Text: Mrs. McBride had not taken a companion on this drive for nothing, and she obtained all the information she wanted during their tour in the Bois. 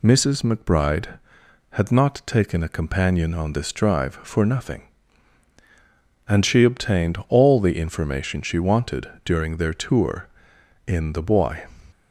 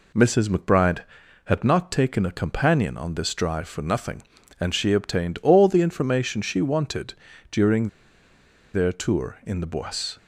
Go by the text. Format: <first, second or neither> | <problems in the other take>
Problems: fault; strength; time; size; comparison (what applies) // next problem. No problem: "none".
first | pauses between "wanted" and "during"; slight; at 7.1 s; 0.36 s long; slight in the first // pauses between "during" and "their"; noticeable; at 7.8 s; 0.85 s long